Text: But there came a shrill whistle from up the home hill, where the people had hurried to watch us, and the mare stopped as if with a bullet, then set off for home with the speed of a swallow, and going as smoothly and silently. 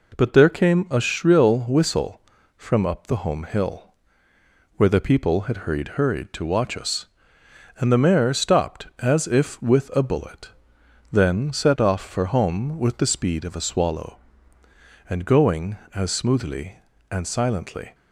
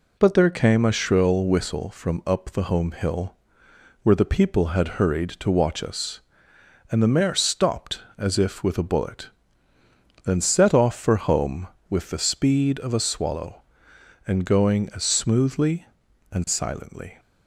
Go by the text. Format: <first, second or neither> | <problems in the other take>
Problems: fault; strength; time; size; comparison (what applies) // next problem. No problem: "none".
second | says "hurried" twice; at 5.9 s